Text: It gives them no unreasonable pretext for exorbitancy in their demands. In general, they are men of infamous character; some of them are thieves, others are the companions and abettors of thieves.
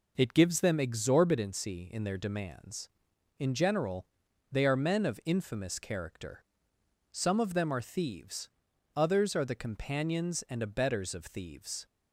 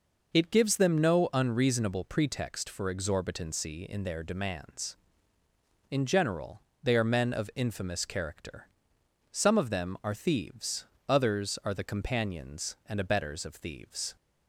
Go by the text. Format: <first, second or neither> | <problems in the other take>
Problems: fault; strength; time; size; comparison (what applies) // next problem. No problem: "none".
second | skips "no unreasonable pretext for"; at 0.7 s